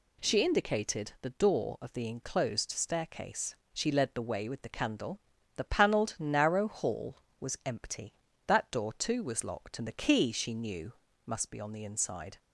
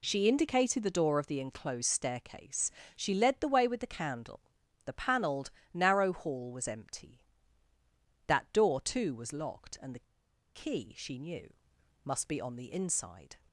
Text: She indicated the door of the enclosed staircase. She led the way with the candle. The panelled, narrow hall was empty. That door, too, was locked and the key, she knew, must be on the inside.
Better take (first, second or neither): first